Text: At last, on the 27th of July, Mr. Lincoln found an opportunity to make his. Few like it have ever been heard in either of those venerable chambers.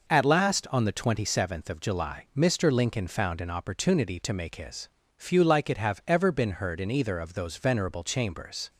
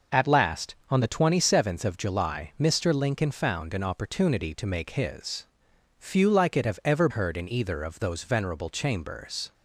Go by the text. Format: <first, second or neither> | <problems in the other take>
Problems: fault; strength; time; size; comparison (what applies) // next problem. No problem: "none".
first | skips "been"; at 7.0 s